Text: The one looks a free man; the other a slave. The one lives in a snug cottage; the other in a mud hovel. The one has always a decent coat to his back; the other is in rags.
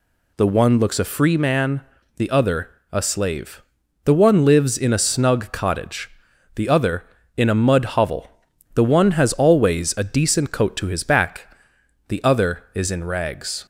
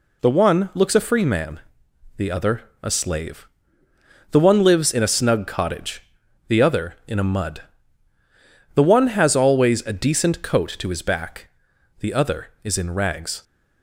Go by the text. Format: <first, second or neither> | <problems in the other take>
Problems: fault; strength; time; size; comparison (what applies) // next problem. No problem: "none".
first | pauses between "other" and "a"; slight; at 2.6 s; 0.18 s long; slight in the first // skips "hovel"; at 8.1 s